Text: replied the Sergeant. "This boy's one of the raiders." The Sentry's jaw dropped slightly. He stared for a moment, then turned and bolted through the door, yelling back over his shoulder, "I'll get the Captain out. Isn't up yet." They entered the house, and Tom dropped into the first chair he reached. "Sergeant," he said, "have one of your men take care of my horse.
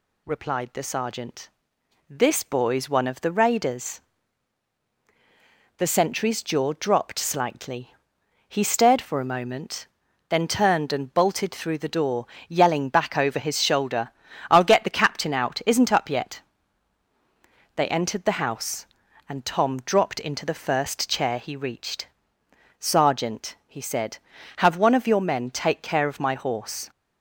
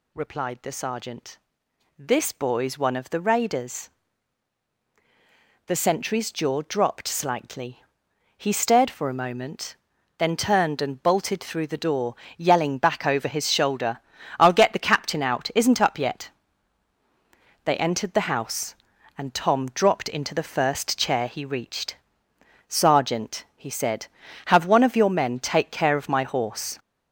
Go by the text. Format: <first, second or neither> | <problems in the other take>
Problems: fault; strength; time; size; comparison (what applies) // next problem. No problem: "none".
first | gets louder; noticeable; throughout; 4.5 dB